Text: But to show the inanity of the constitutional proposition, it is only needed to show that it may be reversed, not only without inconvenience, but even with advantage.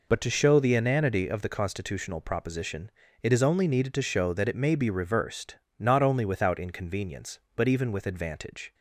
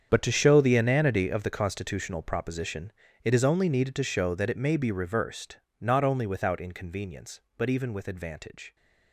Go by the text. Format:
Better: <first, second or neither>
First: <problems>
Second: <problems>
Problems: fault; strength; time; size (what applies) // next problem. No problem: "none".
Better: first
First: none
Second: gets quieter; strong; throughout; 15 dB